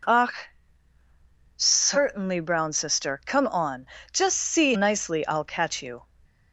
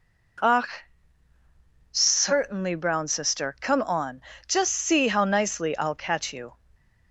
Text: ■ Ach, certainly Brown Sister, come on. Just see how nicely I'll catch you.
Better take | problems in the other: second | skips "how"; at 4.7 s

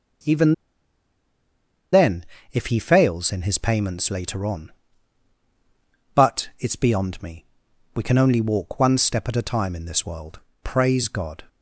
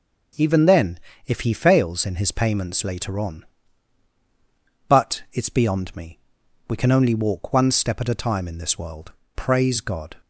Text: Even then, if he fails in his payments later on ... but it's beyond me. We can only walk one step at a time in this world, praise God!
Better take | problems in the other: second | pauses between "Even" and "then"; strong; at 0.5 s; 1.3 s long

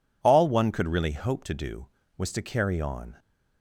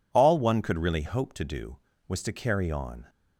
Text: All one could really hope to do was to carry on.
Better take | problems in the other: neither | none

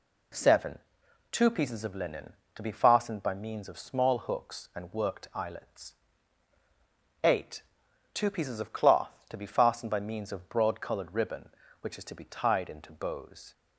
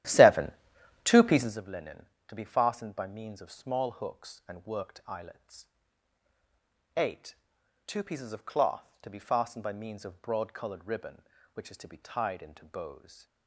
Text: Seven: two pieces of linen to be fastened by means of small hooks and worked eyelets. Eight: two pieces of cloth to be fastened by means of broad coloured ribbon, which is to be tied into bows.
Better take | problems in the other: first | starts louder than the rest; strong; until 1.6 s; 12.5 dB

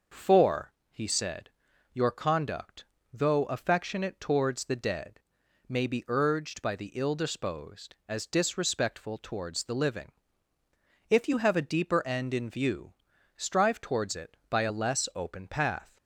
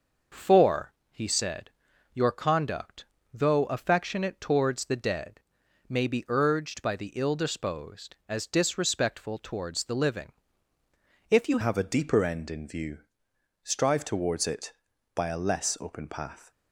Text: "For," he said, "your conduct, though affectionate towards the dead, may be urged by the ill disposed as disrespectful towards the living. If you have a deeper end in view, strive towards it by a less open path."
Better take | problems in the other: first | starts louder than the rest; noticeable; until 1.5 s; 6 dB; noticeable in the first // changes voice at "have"; from 11.6 s on; 4.9 s long

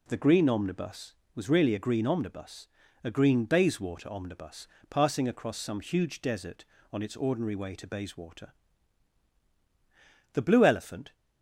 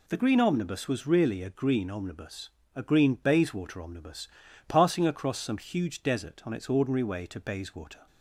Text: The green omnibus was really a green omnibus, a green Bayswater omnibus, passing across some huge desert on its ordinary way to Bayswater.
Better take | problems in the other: second | goes on to say "The blue elephant"; noticeable; from 10.3 s on; 0.80 s long

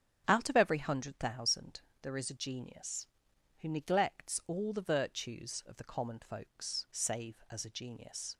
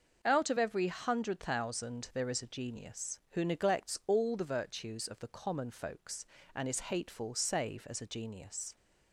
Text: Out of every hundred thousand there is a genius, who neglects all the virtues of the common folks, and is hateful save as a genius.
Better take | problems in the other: second | starts louder than the rest; strong; until 1.2 s; 9 dB // pauses between "thousand" and "there"; slight; at 1.8 s; 0.20 s long // skips "and is hateful"; at 6.8 s

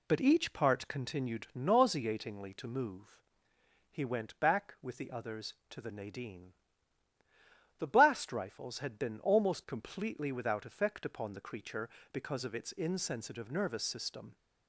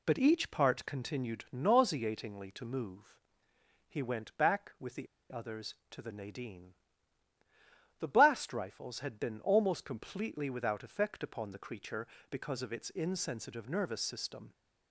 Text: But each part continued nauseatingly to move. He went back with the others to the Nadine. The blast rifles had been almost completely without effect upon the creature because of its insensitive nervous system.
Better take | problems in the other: first | pauses between "the" and "others"; slight; at 5.0 s; 0.23 s long

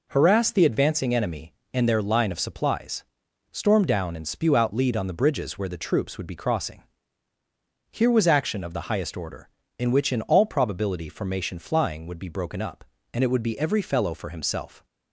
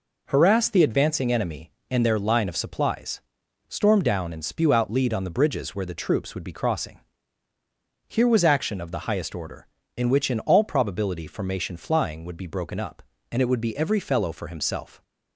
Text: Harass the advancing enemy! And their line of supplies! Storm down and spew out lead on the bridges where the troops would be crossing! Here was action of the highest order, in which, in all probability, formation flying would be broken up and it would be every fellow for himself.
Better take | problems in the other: neither | none

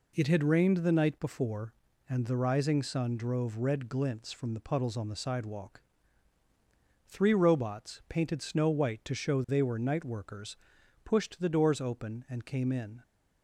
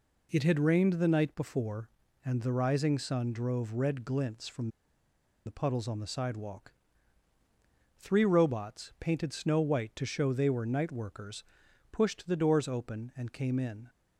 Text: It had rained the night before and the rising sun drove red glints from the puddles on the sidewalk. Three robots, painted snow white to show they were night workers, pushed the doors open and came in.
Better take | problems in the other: first | pauses between "from" and "the"; noticeable; at 4.6 s; 0.77 s long

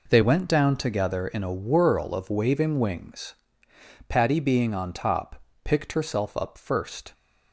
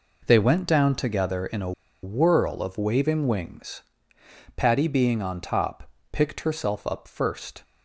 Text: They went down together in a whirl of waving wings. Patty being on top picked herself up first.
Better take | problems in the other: first | pauses between "a" and "whirl"; slight; at 1.7 s; 0.31 s long // pauses between "top" and "picked"; slight; at 5.8 s; 0.22 s long; slight in the first

